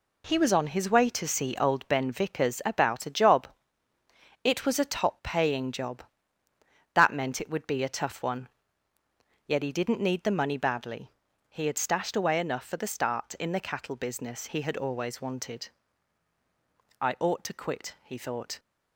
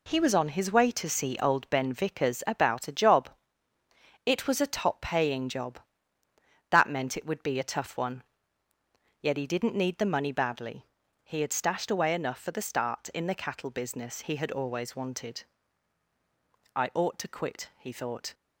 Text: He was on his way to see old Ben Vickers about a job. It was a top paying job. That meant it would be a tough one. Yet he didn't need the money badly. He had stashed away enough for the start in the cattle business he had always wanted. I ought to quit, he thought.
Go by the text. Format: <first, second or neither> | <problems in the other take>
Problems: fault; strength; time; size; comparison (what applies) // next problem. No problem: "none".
neither | none